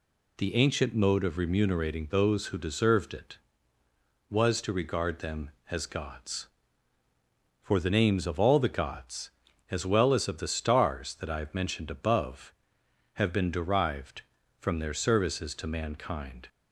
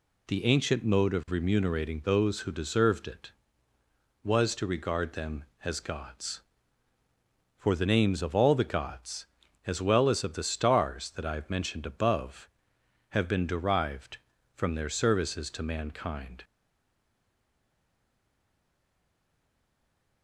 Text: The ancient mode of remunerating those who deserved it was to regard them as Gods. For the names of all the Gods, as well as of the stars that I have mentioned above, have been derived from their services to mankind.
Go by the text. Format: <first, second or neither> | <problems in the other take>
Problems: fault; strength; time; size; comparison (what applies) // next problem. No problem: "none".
first | stays silent after the last word; strong; from 16.4 s on; 3.8 s long